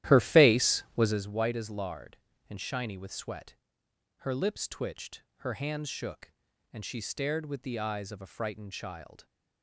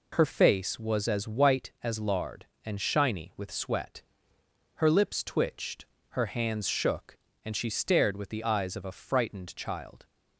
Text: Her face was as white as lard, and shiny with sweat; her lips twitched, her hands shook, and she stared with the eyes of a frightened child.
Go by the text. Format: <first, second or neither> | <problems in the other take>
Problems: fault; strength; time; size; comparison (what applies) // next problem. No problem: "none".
second | starts louder than the rest; strong; until 1.3 s; 13 dB